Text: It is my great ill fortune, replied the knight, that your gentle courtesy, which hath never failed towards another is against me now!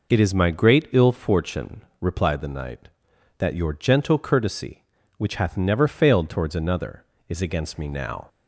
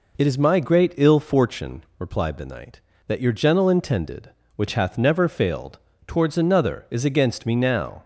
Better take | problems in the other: first | says "intended" for "courtesy"; at 3.6 s // pauses between "failed" and "towards"; slight; at 5.7 s; 0.28 s long

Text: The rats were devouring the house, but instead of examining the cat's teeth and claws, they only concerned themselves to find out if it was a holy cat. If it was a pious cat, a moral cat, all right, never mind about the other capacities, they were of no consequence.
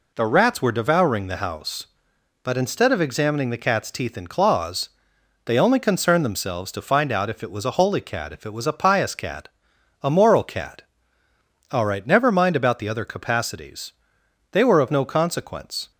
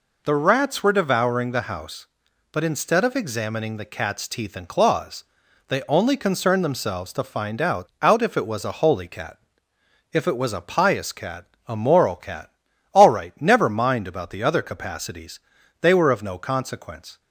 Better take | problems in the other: first | says "out" twice; at 8.0 s

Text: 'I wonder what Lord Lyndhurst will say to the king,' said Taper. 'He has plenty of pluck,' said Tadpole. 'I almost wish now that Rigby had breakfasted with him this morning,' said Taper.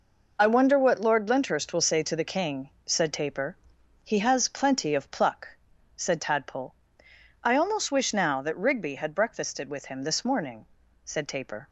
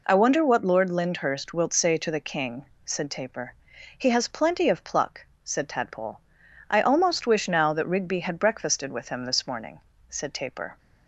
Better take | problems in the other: first | says "wilt" for "will"; at 1.5 s

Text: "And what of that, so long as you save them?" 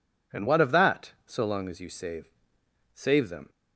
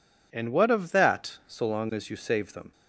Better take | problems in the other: second | says "save" twice; at 2.9 s

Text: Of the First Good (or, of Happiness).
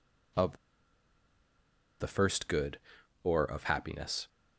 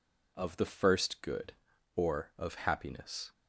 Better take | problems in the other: second | pauses between "Of" and "the"; strong; at 0.5 s; 1.4 s long

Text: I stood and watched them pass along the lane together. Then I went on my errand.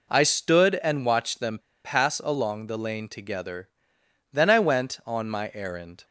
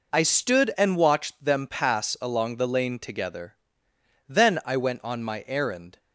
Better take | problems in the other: second | pauses between "them" and "pass"; slight; at 1.5 s; 0.24 s long

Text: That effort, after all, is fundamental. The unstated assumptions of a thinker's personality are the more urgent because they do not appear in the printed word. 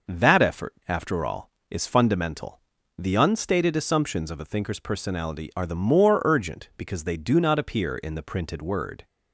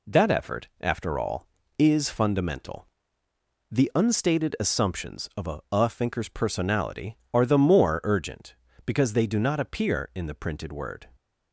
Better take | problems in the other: first | says "a" twice; at 5.7 s

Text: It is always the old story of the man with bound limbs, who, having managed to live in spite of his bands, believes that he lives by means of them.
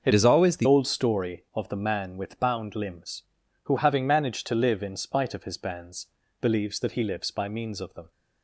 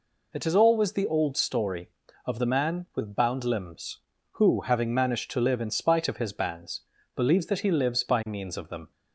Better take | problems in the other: second | starts louder than the rest; until 1.0 s; 6.5 dB // changes voice from "is" to "the"; from 0.1 to 0.6 s; 0.5 s long

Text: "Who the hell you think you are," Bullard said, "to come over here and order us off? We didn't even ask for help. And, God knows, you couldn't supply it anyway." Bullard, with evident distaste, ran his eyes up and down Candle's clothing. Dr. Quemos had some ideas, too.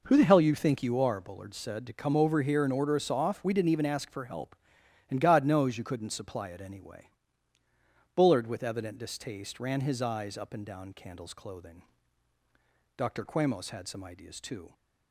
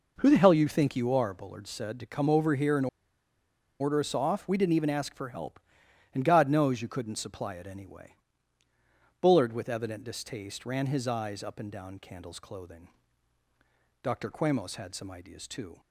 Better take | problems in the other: first | pauses between "and" and "order"; noticeable; at 2.8 s; 0.93 s long

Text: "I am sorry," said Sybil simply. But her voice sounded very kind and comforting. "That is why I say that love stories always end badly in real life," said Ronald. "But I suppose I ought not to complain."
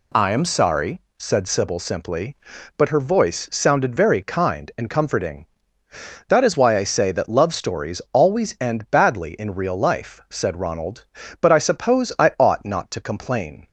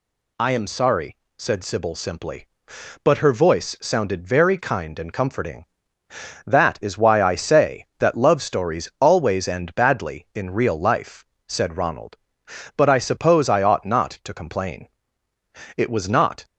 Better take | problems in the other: first | goes on to say "It was not"; noticeable; from 15.7 s on; 0.68 s long

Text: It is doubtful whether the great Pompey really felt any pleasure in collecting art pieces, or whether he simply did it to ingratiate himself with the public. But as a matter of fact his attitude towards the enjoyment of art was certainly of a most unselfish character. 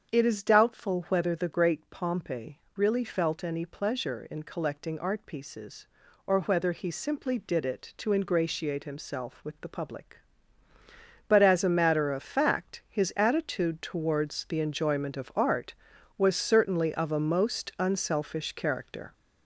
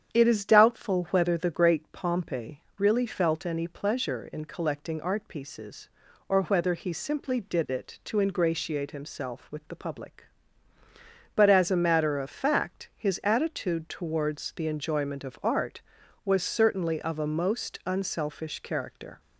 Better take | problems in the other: second | gets louder; throughout; 4 dB // starts louder than the rest; strong; until 1.1 s; 7.5 dB; strong in the second

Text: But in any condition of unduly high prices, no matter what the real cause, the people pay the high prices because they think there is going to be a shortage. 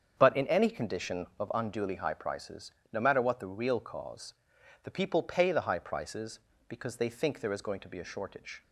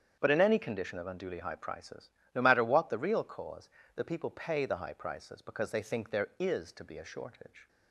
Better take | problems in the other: first | starts louder than the rest; strong; until 1.2 s; 8 dB; strong in the first // skips "going"; at 6.7 s

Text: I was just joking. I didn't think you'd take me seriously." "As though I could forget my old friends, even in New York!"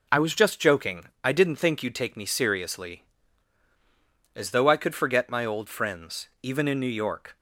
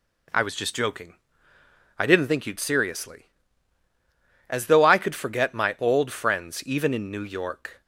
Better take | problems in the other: first | skips "take me"; at 2.5 s

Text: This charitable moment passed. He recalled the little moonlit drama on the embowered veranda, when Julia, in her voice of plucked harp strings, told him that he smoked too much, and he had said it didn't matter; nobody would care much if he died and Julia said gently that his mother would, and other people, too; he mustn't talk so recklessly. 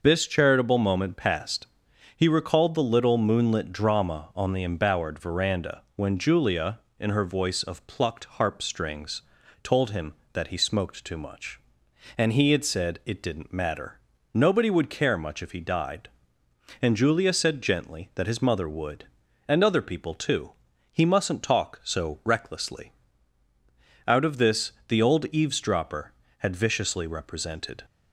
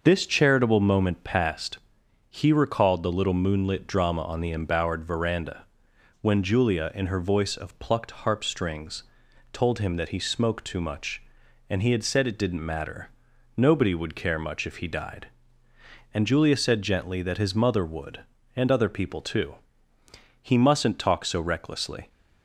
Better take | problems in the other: second | starts louder than the rest; noticeable; until 1.0 s; 6 dB; also in the second // goes on to say "Out of this the old eavesdropper had viciously represented"; strong; from 24.0 s on; 3.7 s long

